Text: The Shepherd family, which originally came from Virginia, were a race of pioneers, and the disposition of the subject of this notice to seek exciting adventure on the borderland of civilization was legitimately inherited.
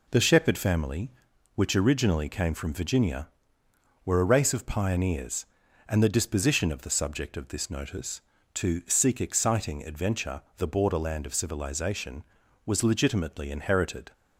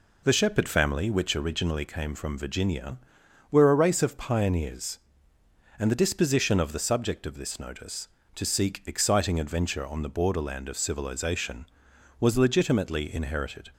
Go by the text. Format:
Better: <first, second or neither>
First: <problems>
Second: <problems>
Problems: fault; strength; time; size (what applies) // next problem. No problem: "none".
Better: second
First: skips "on"; at 10.4 s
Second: none